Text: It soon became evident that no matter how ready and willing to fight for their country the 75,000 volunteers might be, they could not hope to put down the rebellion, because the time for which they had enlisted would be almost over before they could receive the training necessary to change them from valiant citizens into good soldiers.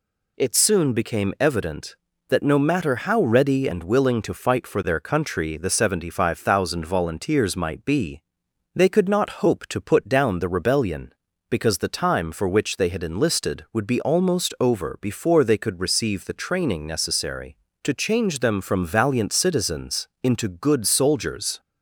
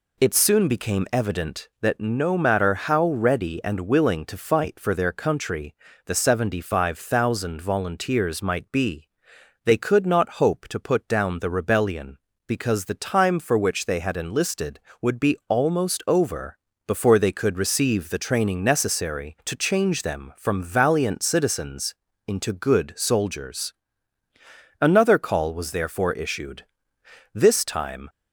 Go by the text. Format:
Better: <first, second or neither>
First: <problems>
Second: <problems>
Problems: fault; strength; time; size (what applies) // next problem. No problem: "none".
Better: first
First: pauses between "citizens" and "into"; slight; at 20.0 s; 0.16 s long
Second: pauses between "country" and "the"; slight; at 5.7 s; 0.30 s long // pauses between "over" and "before"; slight; at 16.5 s; 0.30 s long // pauses between "citizens" and "into"; slight; at 21.9 s; 0.32 s long // goes on to say "Another call was therefore issued this time"; strong; from 24.7 s on; 3.2 s long